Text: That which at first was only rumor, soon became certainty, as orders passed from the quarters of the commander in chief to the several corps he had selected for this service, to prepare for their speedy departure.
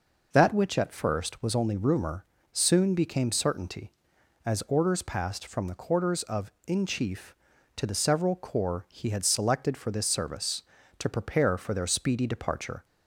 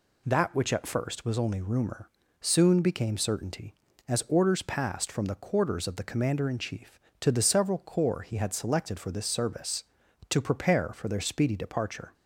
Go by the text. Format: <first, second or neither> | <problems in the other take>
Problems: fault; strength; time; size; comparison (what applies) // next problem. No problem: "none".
second | skips "the commander"; at 6.5 s